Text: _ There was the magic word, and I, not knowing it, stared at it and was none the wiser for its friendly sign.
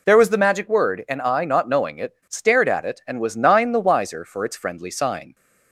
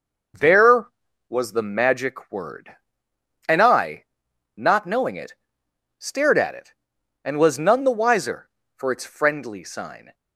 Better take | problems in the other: second | says "nine" for "none"; at 3.3 s

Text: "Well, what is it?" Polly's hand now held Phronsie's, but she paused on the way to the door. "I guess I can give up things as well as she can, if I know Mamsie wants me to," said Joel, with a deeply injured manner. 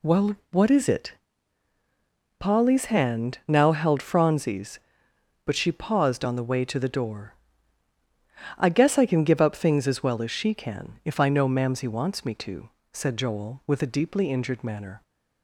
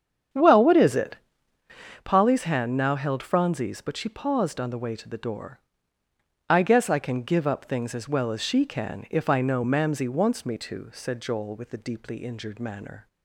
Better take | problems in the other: first | starts louder than the rest; strong; until 1.8 s; 8.5 dB

